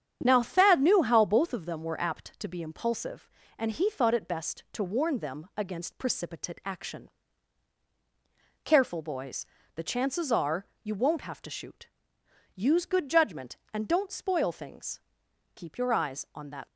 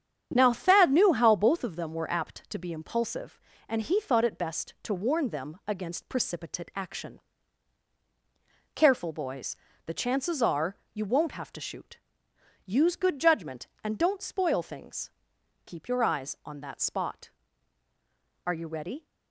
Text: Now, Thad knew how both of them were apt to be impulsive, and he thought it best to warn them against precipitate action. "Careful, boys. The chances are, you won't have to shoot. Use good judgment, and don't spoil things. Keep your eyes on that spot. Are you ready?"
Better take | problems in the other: second | starts louder than the rest; strong; until 1.2 s; 8.5 dB; strong in the second // stops before "spot Are you ready"; at 16.6 s

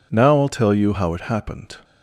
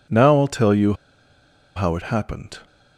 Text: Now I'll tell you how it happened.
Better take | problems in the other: first | pauses between "you" and "how"; noticeable; at 0.9 s; 0.82 s long

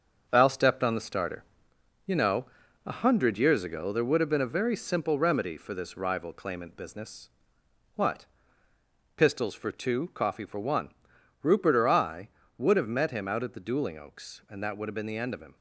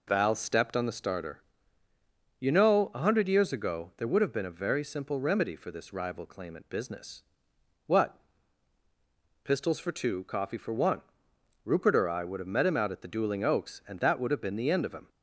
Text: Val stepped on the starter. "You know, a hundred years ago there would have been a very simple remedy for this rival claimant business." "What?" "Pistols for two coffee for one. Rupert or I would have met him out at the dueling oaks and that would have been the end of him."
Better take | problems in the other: second | gets quieter; noticeable; throughout; 6 dB

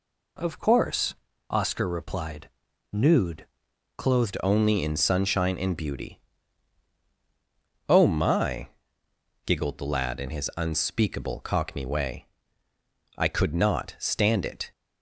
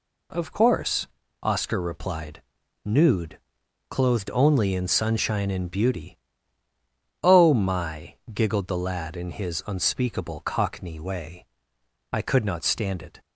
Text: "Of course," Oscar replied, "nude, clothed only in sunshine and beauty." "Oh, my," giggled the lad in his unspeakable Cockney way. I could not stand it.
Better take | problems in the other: second | changes voice at "only"; from 4.4 s on; 10.3 s long

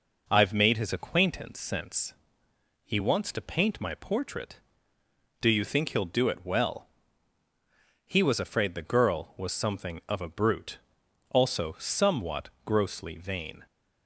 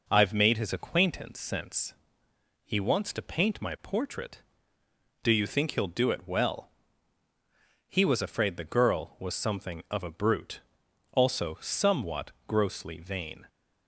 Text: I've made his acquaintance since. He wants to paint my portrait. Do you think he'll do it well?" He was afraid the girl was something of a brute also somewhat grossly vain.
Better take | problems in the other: neither | pauses between "brute" and "also"; noticeable; the same in both // pauses between "somewhat" and "grossly"; slight; the same in both

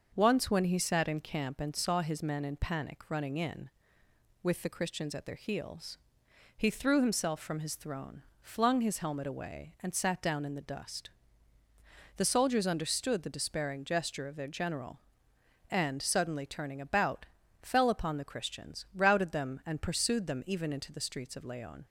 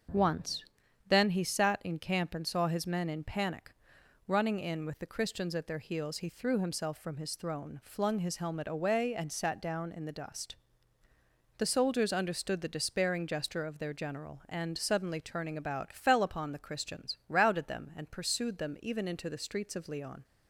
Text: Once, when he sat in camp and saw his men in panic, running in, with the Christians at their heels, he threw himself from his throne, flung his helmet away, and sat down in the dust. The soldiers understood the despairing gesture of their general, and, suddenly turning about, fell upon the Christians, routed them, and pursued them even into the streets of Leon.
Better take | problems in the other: first | starts louder than the rest; until 1.5 s; 6.5 dB; also in the first // says "then" for "when"; at 1.0 s

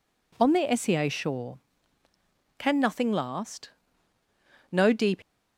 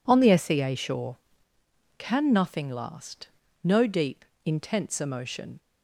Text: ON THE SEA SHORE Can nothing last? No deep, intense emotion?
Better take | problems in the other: second | stops before "intense emotion"; at 5.2 s

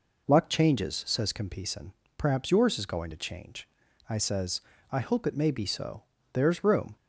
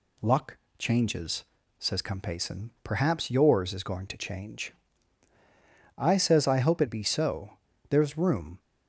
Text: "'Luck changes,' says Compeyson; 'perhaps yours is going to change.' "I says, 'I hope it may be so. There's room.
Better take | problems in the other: first | pauses between "Luck" and "changes"; slight; at 0.5 s; 0.22 s long // skips "may"; at 6.8 s

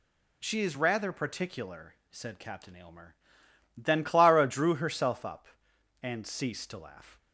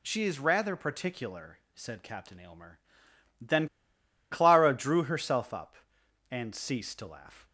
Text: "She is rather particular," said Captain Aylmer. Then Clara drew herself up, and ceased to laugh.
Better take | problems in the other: first | pauses between "Then" and "Clara"; noticeable; at 3.6 s; 0.63 s long

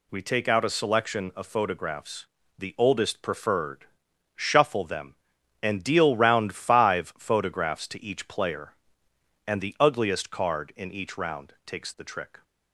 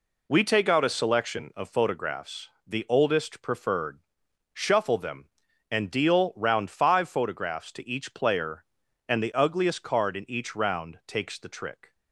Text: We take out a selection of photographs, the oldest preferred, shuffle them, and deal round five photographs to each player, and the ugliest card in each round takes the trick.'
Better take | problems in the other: neither | none

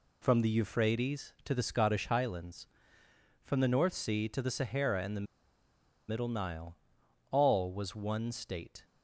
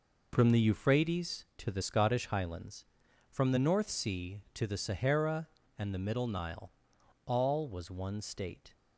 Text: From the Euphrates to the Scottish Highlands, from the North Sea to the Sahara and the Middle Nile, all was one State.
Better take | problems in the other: second | pauses between "the" and "Middle"; noticeable; at 5.2 s; 0.83 s long

